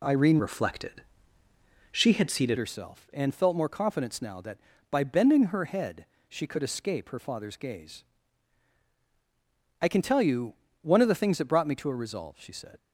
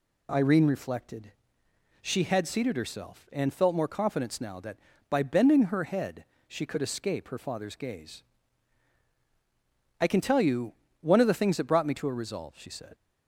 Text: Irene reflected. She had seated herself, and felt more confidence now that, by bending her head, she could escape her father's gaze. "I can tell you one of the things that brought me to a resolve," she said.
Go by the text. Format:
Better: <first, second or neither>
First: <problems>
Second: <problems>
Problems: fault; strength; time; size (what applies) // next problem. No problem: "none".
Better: second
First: changes voice from "reflected" to "seated"; from 0.3 to 2.5 s; 2.2 s long // pauses between "you" and "one"; slight; at 10.5 s; 0.28 s long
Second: pauses between "you" and "one"; slight; at 10.7 s; 0.28 s long